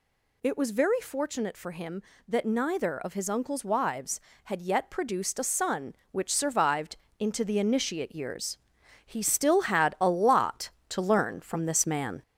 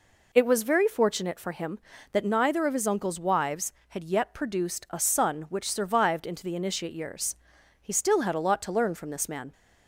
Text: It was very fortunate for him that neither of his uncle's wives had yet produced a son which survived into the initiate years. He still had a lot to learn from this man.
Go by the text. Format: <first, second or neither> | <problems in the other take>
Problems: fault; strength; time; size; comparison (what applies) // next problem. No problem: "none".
second | gets louder; throughout; 4 dB // pauses between "survived" and "into"; slight; at 6.9 s; 0.24 s long